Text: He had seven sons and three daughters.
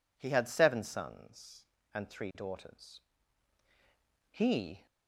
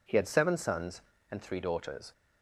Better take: second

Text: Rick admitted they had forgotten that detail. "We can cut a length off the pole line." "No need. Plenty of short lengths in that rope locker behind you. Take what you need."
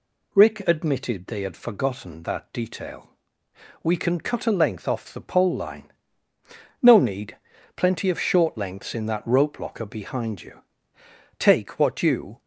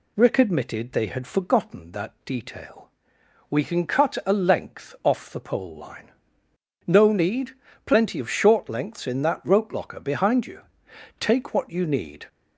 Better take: second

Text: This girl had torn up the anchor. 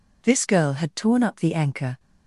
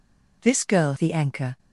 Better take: first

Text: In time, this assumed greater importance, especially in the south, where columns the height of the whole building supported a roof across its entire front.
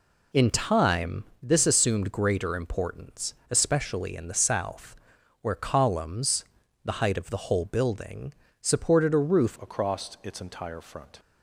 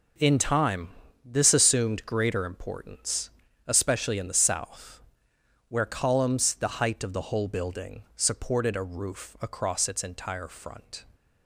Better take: second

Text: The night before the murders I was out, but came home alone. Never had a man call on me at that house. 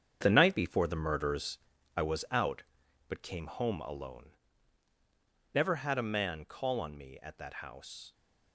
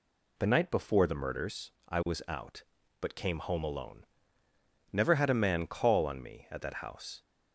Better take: second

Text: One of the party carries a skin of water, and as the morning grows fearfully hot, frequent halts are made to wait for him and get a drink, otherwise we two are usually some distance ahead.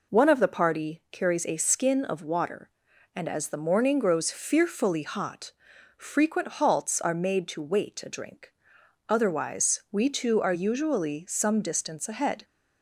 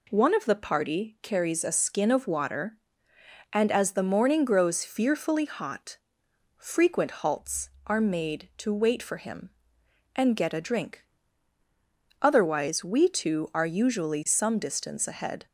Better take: second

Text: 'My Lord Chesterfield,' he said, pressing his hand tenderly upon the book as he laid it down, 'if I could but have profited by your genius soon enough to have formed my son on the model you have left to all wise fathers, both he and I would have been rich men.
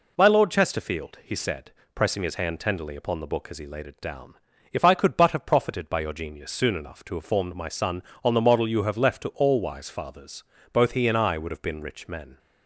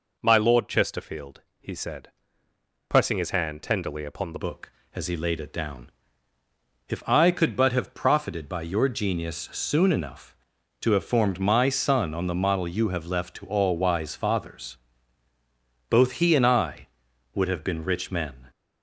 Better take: first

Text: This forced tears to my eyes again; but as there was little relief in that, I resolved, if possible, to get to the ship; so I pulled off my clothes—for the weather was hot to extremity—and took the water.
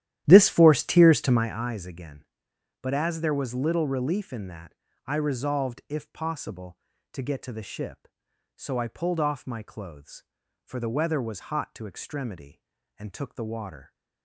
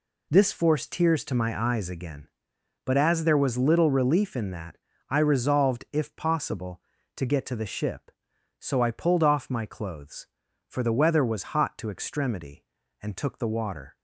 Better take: second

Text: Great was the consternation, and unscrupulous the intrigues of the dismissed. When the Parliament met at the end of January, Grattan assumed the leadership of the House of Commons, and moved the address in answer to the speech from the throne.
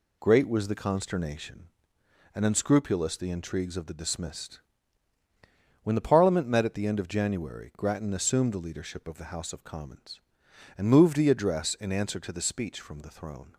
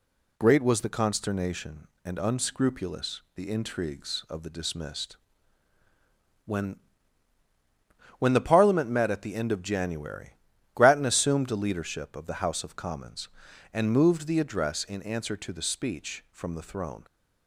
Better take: first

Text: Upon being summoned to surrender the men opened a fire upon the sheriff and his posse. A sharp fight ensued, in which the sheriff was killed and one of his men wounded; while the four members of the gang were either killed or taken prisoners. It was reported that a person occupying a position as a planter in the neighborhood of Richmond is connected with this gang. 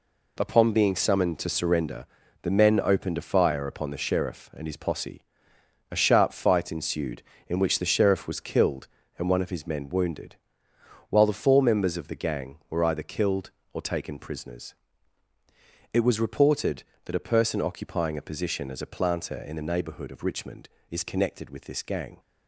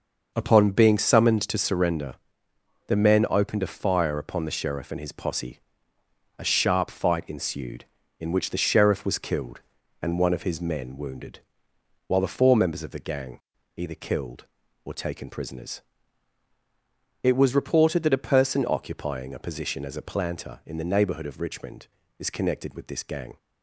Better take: first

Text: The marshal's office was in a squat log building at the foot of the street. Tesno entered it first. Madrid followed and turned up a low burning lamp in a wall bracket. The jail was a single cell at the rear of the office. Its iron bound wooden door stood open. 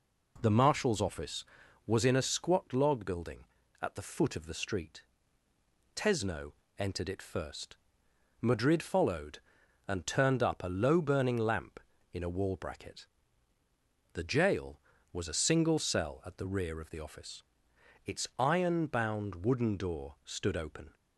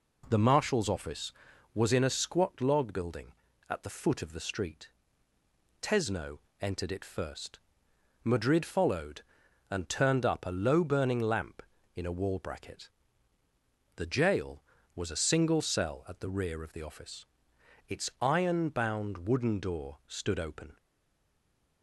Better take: first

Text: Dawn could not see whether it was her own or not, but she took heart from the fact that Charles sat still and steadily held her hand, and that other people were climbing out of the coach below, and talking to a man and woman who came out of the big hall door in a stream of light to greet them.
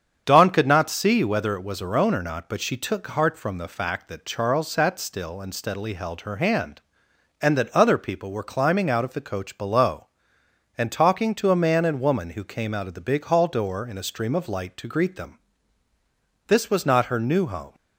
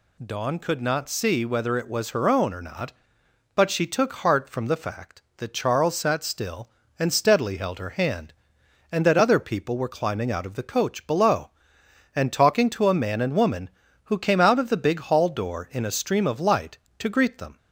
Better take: second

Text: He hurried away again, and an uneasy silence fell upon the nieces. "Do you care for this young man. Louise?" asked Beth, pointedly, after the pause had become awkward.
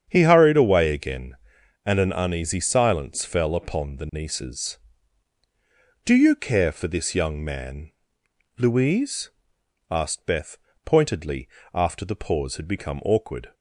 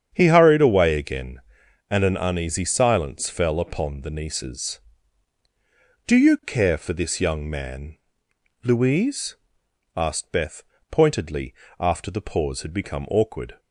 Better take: neither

